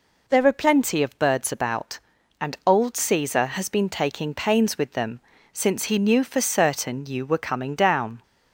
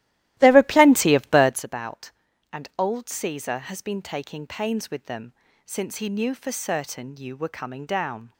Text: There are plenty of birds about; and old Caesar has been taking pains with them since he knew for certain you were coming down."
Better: first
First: pauses between "them" and "since"; slight; at 5.2 s; 0.32 s long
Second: starts louder than the rest; strong; until 1.6 s; 15 dB // pauses between "them" and "since"; slight; at 5.3 s; 0.32 s long

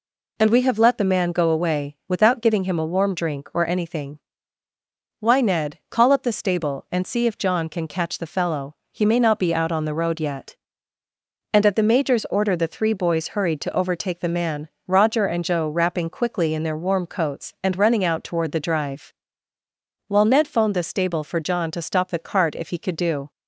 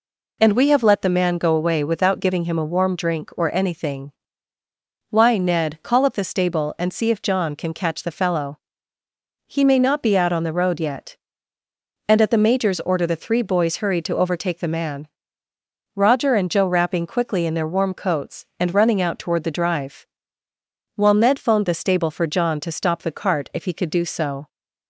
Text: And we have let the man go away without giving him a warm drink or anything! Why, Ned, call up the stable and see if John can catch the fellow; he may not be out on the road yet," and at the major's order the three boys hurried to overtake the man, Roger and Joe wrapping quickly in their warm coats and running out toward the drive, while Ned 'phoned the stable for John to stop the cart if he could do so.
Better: second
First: stops before "so"; at 23.3 s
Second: none

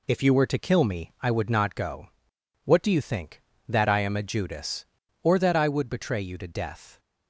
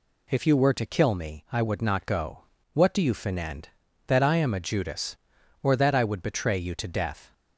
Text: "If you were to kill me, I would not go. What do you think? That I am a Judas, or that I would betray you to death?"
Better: first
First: none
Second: says "finend" for "think"; at 3.1 s

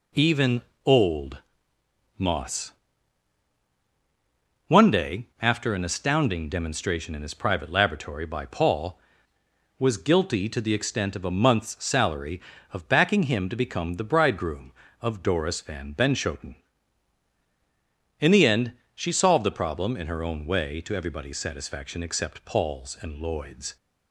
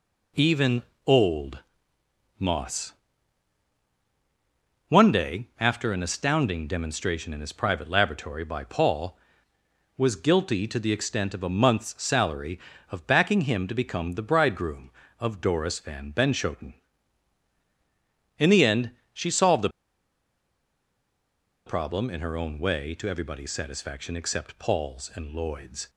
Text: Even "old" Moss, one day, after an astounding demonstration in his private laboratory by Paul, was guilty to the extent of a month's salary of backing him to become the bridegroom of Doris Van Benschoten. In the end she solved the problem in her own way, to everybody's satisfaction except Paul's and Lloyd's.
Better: first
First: pauses between "Even" and "old"; slight; at 0.6 s; 0.24 s long // pauses between "old" and "Moss"; noticeable; at 1.3 s; 0.80 s long // pauses between "end" and "she"; slight; at 18.7 s; 0.22 s long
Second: pauses between "Even" and "old"; slight; at 0.8 s; 0.24 s long // pauses between "old" and "Moss"; noticeable; at 1.5 s; 0.80 s long // pauses between "end" and "she"; slight; at 18.9 s; 0.22 s long // pauses between "the" and "problem"; strong; at 19.6 s; 1.9 s long

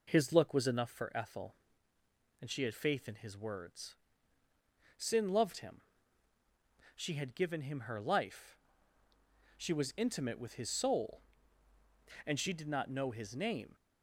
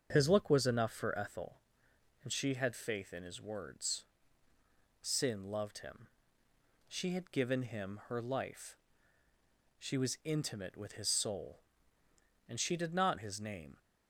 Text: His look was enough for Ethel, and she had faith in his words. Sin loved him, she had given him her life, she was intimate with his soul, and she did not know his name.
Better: first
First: none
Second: starts louder than the rest; strong; until 1.1 s; 7 dB // skips "know"; at 13.1 s

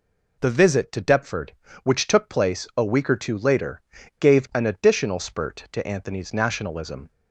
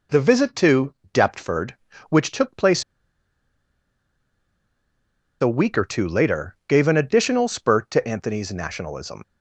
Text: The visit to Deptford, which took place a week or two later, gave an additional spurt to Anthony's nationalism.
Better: first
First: none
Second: pauses between "to" and "Deptford"; slight; at 0.9 s; 0.18 s long // pauses between "place" and "a"; strong; at 2.8 s; 2.5 s long

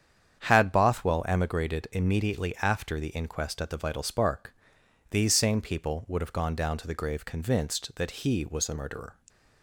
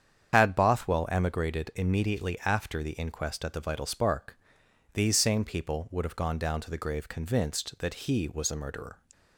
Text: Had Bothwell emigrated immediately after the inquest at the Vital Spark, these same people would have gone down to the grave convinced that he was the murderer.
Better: first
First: starts louder than the rest; strong; until 1.4 s; 8.5 dB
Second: loses the start of "Had"; at 0.3 s; 90 ms // starts louder than the rest; strong; until 1.3 s; 8 dB

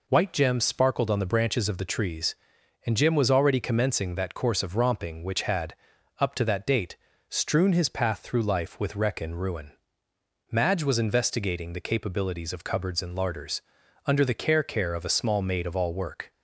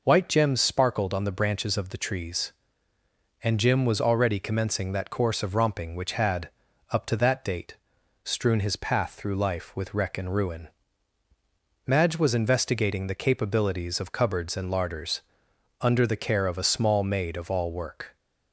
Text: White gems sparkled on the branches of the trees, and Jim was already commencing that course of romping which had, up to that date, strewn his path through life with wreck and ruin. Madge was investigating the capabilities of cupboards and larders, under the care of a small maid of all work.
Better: second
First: says "care" twice; at 14.6 s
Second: none

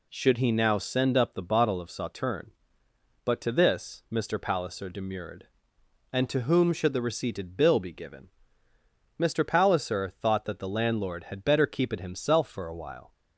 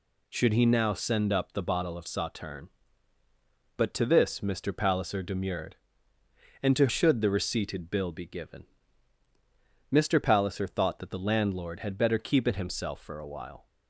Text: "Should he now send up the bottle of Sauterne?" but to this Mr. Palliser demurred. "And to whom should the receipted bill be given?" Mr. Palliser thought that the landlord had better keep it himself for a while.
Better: first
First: none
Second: skips "whom"; at 6.8 s

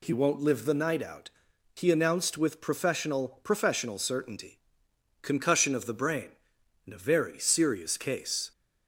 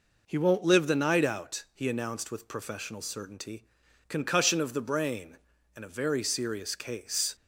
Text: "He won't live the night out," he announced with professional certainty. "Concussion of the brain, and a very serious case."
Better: second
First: says "professional" twice; at 3.4 s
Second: none

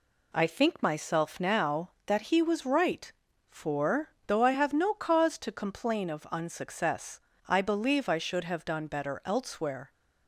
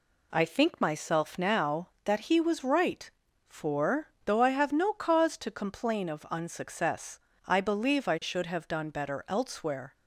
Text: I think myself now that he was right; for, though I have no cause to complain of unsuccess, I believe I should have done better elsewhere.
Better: neither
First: none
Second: none

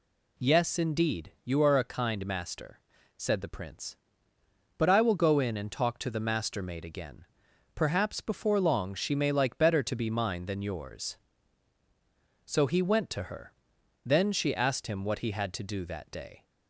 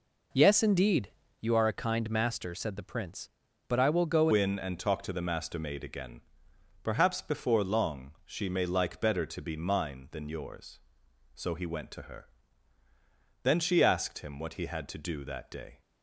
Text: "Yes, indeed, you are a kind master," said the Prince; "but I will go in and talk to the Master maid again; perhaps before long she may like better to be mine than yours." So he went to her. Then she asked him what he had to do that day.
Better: first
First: none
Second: changes voice at "in"; from 4.3 s on; 11.5 s long

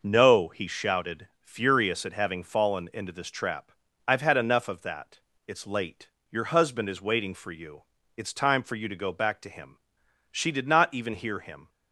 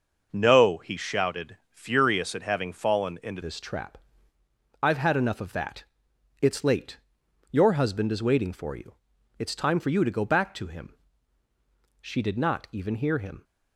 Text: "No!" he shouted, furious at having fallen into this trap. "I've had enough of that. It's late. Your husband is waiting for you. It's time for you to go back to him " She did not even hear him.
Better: first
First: none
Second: changes voice at "this"; from 3.4 s on; 10.0 s long

